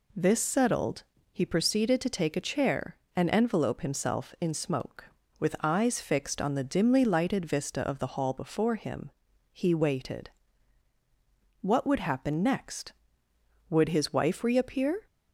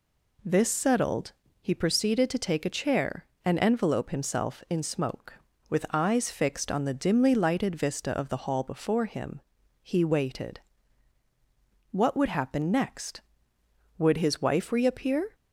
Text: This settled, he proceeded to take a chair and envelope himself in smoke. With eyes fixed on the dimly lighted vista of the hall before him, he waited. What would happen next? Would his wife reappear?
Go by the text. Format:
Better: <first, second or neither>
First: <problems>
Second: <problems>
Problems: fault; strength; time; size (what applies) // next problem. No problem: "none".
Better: neither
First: none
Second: none